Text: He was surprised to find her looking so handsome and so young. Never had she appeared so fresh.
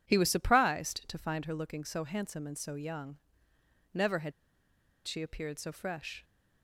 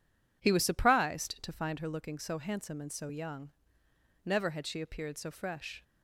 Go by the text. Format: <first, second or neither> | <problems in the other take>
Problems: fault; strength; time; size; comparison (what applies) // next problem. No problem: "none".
second | pauses between "had" and "she"; noticeable; at 4.3 s; 0.75 s long